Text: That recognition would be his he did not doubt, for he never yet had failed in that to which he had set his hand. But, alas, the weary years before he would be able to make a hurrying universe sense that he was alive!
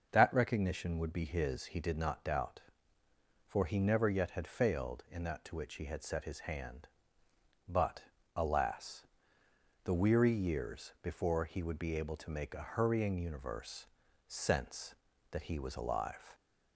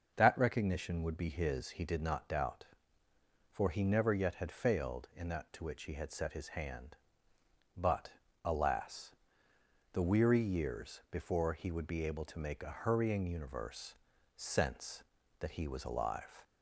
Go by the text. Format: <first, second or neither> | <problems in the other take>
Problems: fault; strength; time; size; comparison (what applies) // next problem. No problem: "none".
neither | starts louder than the rest; the same in both // pauses between "universe" and "sense"; the same in both